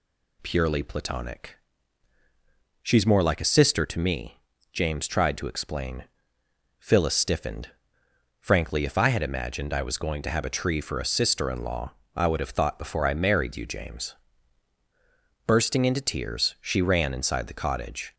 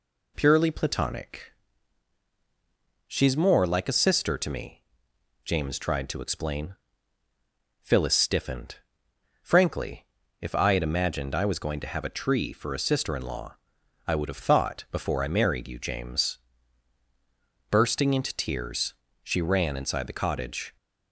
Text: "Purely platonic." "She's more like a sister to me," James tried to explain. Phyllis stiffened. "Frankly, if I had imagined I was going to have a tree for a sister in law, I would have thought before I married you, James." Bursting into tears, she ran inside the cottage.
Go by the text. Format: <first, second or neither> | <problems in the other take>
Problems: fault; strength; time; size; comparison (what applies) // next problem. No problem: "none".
neither | none